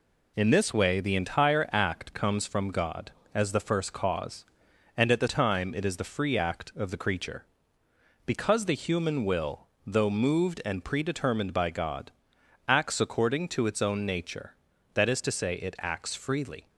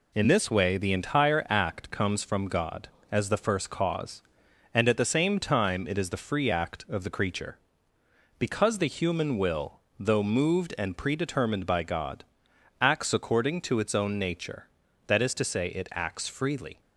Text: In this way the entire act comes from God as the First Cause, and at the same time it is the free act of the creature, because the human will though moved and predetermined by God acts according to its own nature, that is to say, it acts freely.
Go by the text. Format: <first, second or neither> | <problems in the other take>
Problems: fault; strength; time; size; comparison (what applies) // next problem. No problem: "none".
second | skips "same"; at 5.2 s // pauses between "will" and "though"; slight; at 9.6 s; 0.18 s long; slight in the second // pauses between "God" and "acts"; noticeable; at 12.1 s; 0.56 s long; noticeable in the second